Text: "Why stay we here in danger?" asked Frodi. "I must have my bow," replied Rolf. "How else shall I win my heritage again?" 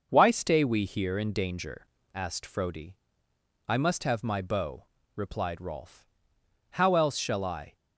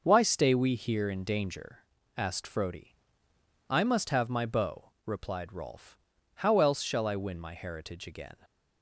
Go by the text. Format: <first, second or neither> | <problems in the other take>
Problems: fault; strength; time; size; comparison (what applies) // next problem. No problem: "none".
second | starts louder than the rest; noticeable; until 1.1 s; 6 dB // stops before "win my heritage again"; at 7.7 s